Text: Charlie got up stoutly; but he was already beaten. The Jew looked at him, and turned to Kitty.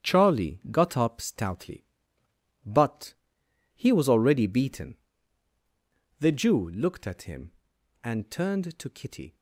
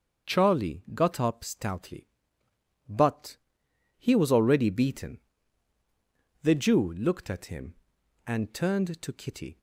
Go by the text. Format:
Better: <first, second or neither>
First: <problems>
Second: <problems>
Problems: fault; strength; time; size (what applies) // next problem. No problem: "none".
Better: second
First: gets quieter; strong; throughout; 10 dB // starts louder than the rest; strong; until 1.1 s; 9.5 dB // pauses between "but" and "he"; noticeable; at 3.1 s; 0.62 s long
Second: starts louder than the rest; until 1.4 s; 7 dB // pauses between "but" and "he"; noticeable; at 3.3 s; 0.62 s long